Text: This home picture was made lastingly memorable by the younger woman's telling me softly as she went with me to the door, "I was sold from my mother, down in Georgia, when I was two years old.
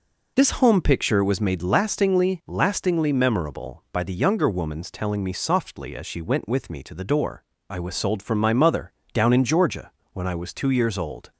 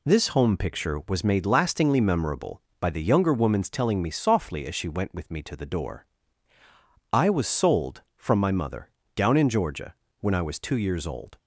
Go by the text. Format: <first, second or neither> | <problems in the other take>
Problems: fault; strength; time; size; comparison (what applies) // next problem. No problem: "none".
second | says "lastingly" twice; at 2.4 s